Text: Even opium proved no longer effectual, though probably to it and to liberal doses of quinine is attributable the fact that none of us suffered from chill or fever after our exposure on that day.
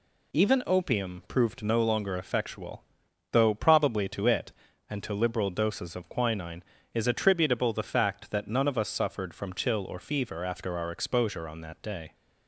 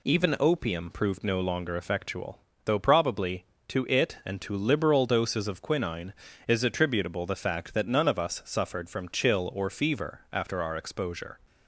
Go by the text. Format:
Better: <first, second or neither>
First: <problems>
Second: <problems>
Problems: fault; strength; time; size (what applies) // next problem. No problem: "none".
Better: first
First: none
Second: stops before "on that day"; at 11.4 s